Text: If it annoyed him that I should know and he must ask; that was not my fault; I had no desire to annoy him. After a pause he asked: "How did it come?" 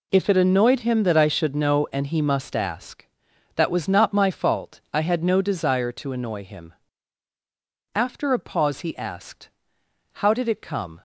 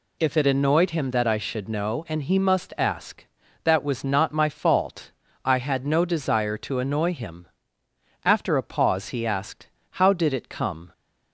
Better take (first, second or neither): neither